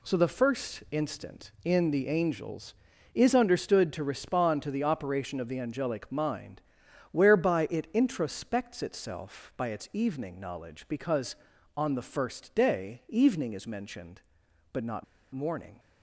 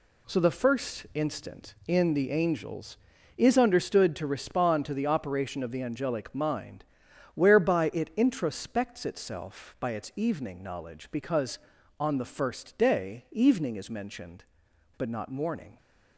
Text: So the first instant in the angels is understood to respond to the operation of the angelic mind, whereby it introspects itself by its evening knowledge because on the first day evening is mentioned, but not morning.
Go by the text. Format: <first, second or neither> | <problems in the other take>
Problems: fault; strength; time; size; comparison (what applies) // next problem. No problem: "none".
second | pauses between "not" and "morning"; slight; at 15.0 s; 0.29 s long